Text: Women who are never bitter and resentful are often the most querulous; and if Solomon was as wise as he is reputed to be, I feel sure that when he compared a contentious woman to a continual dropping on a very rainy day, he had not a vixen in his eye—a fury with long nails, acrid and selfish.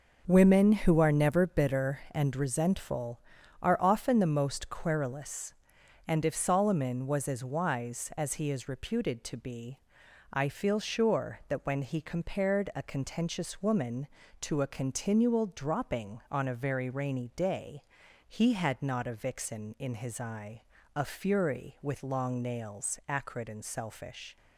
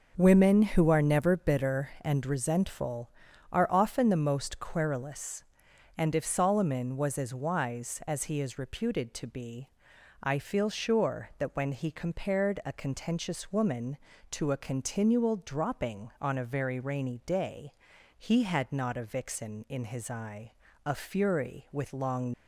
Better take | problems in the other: first | stops before "nails acrid and selfish"; at 22.3 s

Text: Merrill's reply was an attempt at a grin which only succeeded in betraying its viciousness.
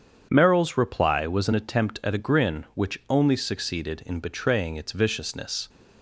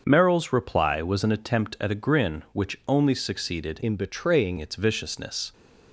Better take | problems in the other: first | starts louder than the rest; until 1.0 s; 7 dB; strong in the first // changes voice from "in" to "betraying"; from 3.8 to 4.5 s; 0.7 s long

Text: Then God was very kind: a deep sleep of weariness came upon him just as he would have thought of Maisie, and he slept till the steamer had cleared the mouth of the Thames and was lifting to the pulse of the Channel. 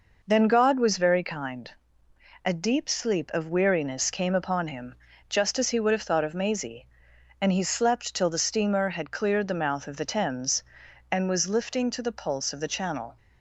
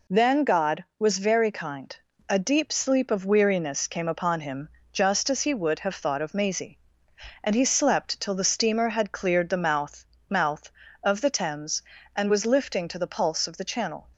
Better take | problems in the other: first | pauses between "him" and "just"; slight; at 4.6 s; 0.24 s long; slight in the first // says "mouth" twice; at 10.2 s

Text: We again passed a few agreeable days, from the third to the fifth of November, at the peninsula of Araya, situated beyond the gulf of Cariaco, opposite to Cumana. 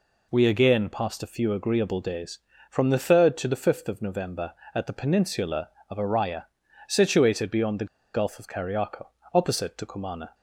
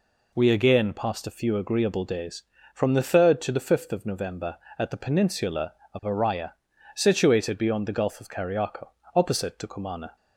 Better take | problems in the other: second | pauses between "the" and "gulf"; slight; at 7.8 s; 0.27 s long

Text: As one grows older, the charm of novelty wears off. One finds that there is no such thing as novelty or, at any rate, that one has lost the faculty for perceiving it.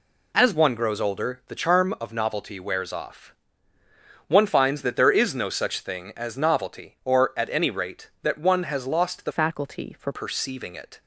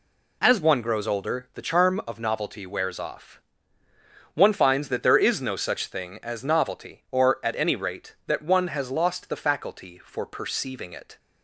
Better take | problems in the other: second | changes voice from "faculty" to "for"; from 9.3 to 10.1 s; 0.8 s long

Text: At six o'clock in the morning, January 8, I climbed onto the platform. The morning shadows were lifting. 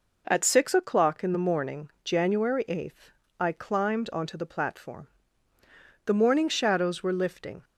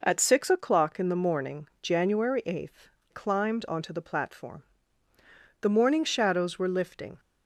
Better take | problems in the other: first | skips "I"; at 2.9 s

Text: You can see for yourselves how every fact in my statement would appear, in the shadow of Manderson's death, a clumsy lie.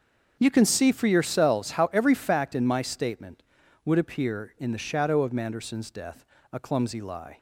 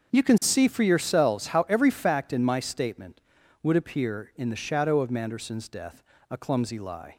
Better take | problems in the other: neither | starts louder than the rest; the same in both

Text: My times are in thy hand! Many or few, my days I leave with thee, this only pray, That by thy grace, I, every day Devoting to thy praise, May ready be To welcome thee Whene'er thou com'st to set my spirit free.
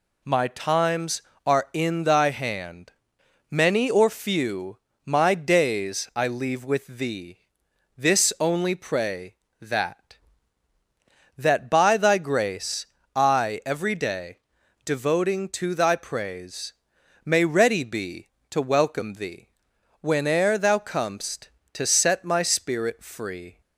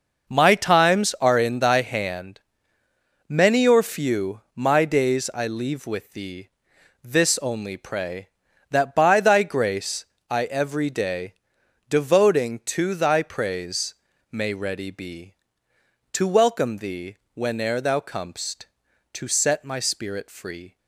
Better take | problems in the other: second | says "That" twice; at 11.3 s // pauses between "day" and "Devoting"; noticeable; at 14.3 s; 0.48 s long; noticeable in the second // pauses between "thee" and "Whene'er"; noticeable; at 19.4 s; 0.54 s long; slight in the second

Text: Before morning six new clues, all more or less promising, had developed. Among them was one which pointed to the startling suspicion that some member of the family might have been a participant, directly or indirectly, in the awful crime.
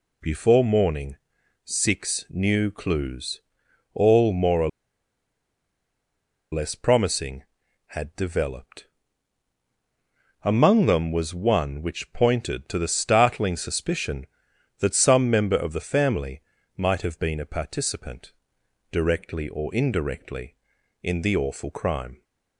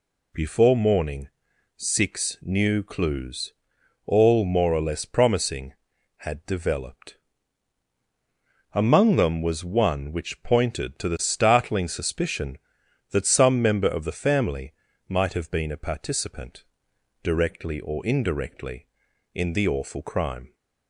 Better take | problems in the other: second | pauses between "morning" and "six"; noticeable; at 1.1 s; 0.50 s long; noticeable in the second // pauses between "or" and "less"; strong; at 4.6 s; 1.8 s long // pauses between "family" and "might"; slight; at 16.4 s; 0.34 s long; slight in the second

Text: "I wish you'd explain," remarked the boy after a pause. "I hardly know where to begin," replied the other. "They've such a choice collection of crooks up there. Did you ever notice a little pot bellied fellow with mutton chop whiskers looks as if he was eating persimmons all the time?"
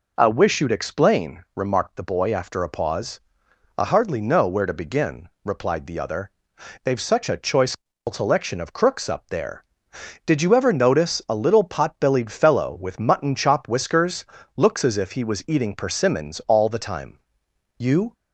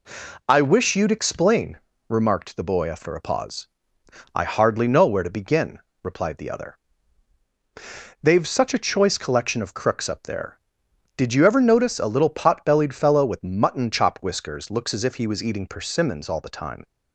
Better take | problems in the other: second | pauses between "choice" and "collection"; at 7.7 s; 0.38 s long // pauses between "whiskers" and "looks"; slight; at 14.2 s; 0.28 s long // goes on to say "You"; slight; from 17.7 s on; 0.36 s long

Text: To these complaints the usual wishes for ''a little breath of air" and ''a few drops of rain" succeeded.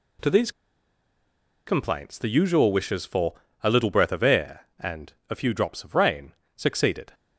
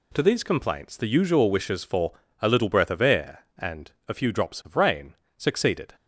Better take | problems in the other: second | pauses between "these" and "complaints"; at 0.5 s; 1.1 s long // pauses between "for" and "a"; slight; at 3.3 s; 0.30 s long; slight in the second // pauses between "and" and "a"; slight; at 5.1 s; 0.16 s long; slight in the second // pauses between "rain" and "succeeded"; slight; at 6.3 s; 0.22 s long; slight in the second

